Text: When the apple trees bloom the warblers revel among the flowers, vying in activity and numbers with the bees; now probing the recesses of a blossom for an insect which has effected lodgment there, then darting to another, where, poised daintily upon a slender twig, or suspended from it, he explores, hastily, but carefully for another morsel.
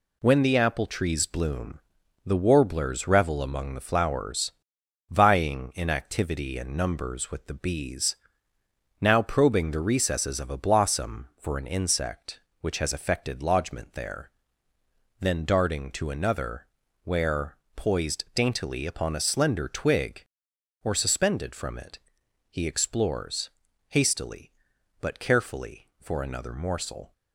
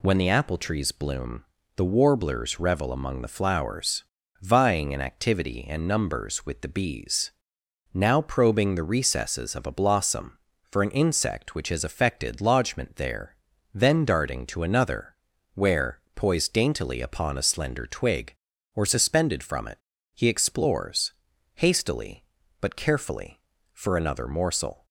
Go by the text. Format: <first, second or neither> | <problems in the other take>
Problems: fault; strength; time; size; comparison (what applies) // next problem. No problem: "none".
second | gets quieter; noticeable; throughout; 5 dB // pauses between "bloom" and "the"; noticeable; at 1.7 s; 0.48 s long; slight in the second